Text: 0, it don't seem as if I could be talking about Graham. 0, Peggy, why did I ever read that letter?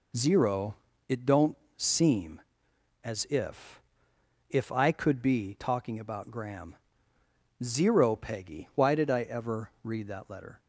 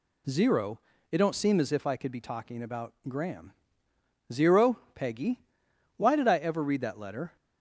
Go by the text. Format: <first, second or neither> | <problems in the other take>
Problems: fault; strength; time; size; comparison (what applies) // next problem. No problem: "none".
second | pauses between "don't" and "seem"; slight; at 1.5 s; 0.22 s long // says "if" twice; at 4.4 s